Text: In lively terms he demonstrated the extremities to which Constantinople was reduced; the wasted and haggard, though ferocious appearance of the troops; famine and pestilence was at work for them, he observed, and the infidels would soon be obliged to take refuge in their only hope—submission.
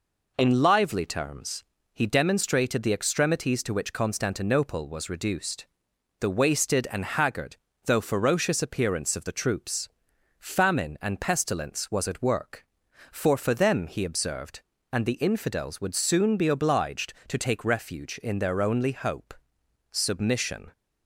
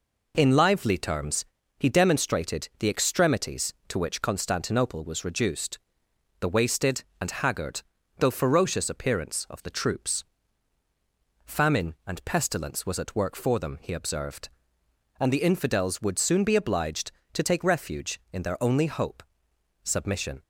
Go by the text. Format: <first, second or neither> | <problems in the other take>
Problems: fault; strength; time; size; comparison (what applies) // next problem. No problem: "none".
second | pauses between "terms" and "he"; slight; at 1.6 s; 0.30 s long; slight in the second // says "for" twice; at 13.3 s